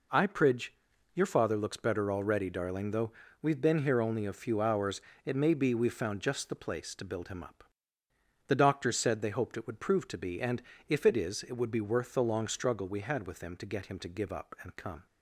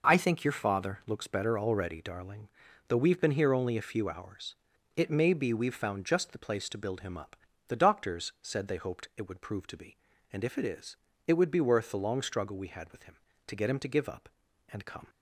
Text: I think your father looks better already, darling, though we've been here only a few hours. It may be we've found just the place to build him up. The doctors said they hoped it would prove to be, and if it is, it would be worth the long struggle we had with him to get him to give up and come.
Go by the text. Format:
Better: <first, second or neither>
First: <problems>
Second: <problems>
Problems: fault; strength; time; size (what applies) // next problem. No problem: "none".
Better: second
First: says "pridge" for "think"; at 0.2 s // pauses between "though" and "we've"; slight; at 3.1 s; 0.30 s long // pauses between "and" and "if"; slight; at 10.6 s; 0.28 s long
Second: none